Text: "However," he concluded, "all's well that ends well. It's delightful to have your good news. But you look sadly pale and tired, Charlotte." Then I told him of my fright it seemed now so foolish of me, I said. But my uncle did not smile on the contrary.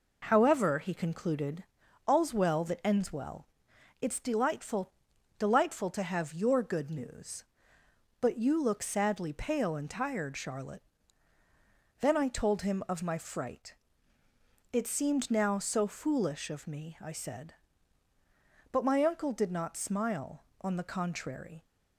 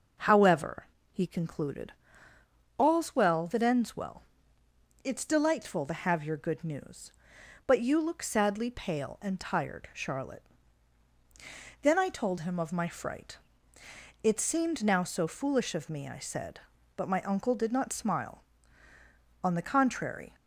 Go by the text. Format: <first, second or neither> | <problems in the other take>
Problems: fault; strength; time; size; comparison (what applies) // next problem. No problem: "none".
second | says "delightful" twice; at 5.3 s // pauses between "fright" and "it"; noticeable; at 13.7 s; 0.96 s long; noticeable in the second